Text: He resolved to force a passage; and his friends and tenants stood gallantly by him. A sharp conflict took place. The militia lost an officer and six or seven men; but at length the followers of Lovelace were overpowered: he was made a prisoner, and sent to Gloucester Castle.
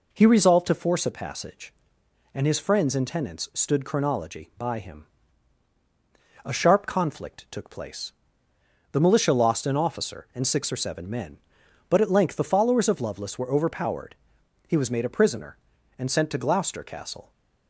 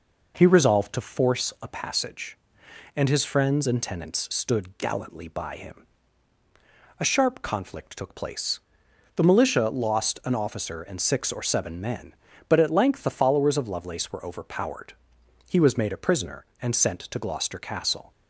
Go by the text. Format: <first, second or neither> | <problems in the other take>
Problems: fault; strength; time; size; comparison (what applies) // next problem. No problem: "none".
second | says "chronology" for "gallantly"; at 3.8 s